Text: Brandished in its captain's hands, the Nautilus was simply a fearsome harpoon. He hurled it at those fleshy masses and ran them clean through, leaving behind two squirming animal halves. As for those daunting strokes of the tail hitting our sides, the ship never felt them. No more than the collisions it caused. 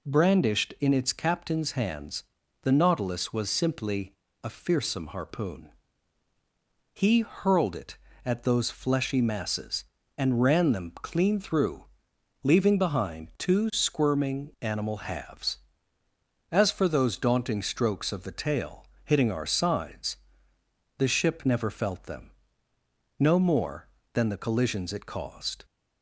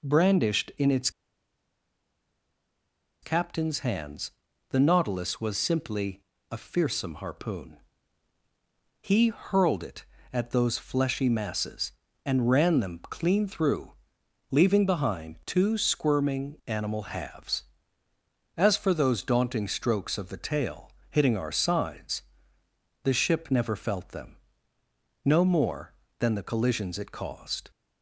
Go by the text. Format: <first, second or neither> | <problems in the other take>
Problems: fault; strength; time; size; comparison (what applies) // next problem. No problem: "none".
first | pauses between "its" and "captain's"; strong; at 1.1 s; 2.1 s long // pauses between "simply" and "a"; slight; at 6.2 s; 0.28 s long; slight in the first // pauses between "tail" and "hitting"; slight; at 20.9 s; 0.20 s long; slight in the first